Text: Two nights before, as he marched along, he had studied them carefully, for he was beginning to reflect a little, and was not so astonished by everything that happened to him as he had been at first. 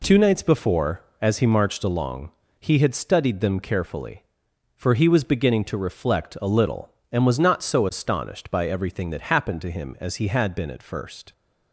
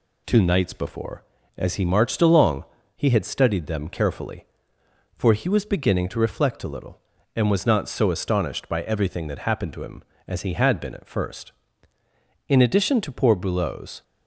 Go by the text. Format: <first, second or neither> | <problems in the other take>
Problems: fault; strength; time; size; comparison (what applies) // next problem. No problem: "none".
first | goes on to say "In addition to poor Boulot's"; from 12.4 s on; 1.5 s long